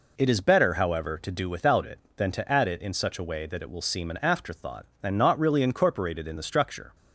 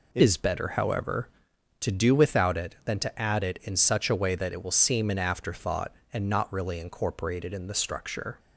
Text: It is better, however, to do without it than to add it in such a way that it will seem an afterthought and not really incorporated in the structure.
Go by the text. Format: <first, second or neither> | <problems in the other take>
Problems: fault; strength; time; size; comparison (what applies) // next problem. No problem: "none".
first | changes voice at "is"; from 0.2 s on; 8.1 s long